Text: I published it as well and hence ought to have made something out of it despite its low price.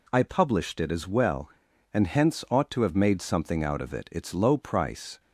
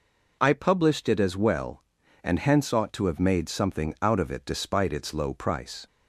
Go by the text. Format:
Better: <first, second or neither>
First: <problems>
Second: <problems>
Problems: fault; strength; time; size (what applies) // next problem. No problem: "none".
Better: second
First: skips "despite"; at 4.0 s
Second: none